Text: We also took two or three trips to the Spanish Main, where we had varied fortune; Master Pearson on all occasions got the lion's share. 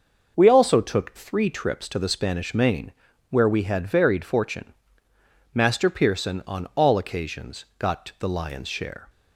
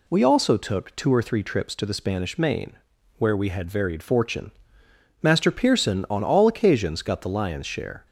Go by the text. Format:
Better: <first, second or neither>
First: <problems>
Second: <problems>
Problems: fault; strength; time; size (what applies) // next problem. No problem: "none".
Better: second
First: skips "two or"; at 1.1 s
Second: none